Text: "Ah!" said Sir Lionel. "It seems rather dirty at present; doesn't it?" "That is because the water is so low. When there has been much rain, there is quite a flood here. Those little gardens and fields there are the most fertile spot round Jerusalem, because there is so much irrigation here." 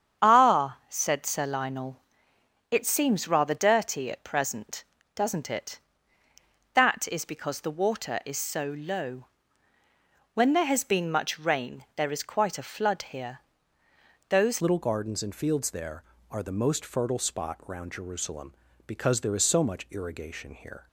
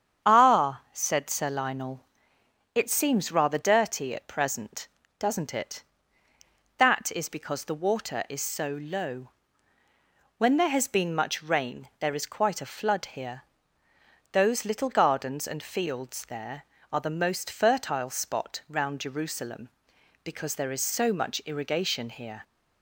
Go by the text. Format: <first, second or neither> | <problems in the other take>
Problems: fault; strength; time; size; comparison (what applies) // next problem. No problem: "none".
second | starts louder than the rest; strong; until 1.2 s; 8.5 dB; strong in the second // changes voice at "little"; from 14.6 s on; 6.2 s long